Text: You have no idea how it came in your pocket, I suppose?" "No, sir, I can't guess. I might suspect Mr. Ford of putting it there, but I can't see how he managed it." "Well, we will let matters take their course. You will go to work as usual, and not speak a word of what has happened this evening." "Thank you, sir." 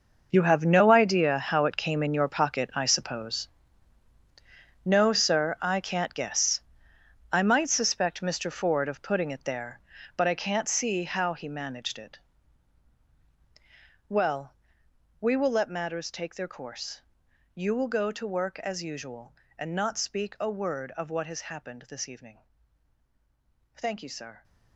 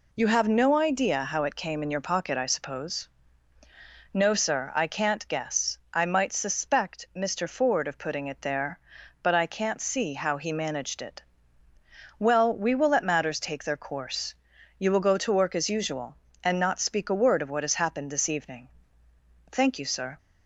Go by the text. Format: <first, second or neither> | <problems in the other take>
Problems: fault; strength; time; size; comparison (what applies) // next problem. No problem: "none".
second | gets quieter; strong; throughout; 14 dB